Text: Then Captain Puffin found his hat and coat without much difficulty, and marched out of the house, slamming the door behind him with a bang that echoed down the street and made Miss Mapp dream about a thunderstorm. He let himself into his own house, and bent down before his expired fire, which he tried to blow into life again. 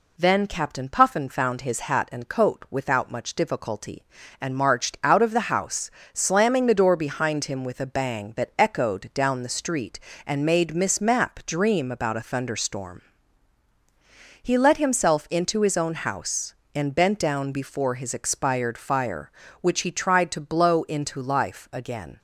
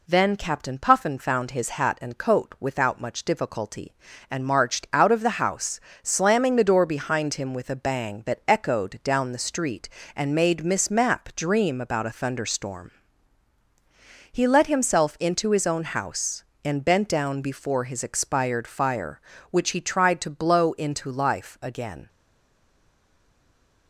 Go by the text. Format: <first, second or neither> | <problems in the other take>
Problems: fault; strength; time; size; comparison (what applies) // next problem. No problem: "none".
first | stays silent after the last word; noticeable; from 22.0 s on; 1.8 s long